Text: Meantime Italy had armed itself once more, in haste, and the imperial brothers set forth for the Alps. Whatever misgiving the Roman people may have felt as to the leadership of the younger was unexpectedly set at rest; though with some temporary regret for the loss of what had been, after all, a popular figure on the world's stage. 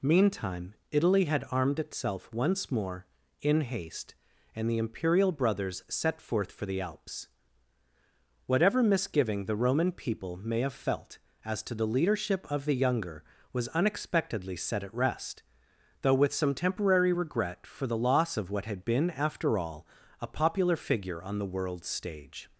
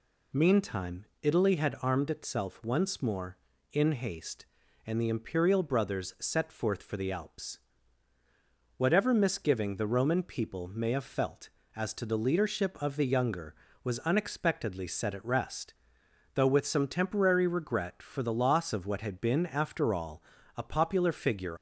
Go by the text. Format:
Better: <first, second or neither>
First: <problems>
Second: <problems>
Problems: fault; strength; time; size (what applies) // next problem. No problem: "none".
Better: first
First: pauses between "Meantime" and "Italy"; slight; at 0.7 s; 0.18 s long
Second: pauses between "Meantime" and "Italy"; slight; at 1.0 s; 0.18 s long // stops before "on the world's stage"; at 21.5 s